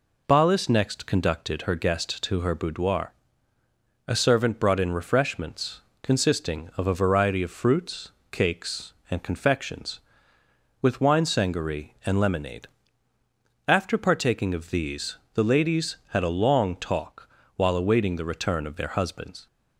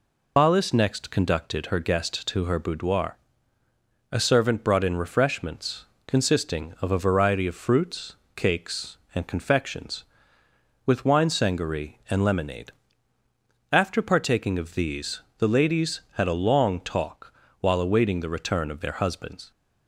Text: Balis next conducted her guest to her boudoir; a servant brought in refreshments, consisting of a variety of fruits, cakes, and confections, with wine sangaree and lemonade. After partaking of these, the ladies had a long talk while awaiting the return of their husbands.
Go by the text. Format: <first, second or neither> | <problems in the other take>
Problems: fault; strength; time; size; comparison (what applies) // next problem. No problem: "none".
first | loses the start of "Balis"; at 0.3 s; 55 ms // pauses between "talk" and "while"; slight; at 17.3 s; 0.28 s long; slight in the first